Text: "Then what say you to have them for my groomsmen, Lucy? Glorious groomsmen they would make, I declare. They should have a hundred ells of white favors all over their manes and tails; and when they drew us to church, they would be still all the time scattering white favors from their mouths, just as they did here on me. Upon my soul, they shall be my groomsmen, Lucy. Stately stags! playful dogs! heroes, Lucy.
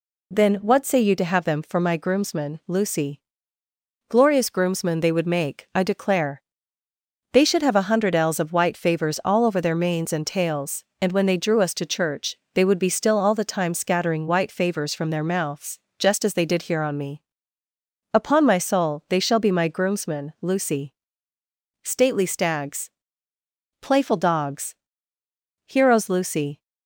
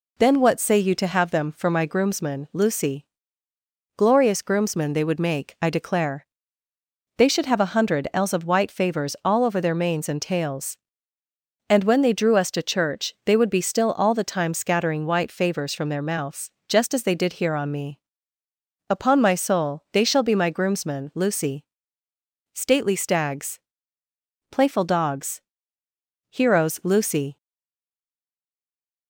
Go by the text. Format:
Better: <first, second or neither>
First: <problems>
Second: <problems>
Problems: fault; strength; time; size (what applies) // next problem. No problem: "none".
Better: first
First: none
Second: stays silent after the last word; noticeable; from 27.3 s on; 1.7 s long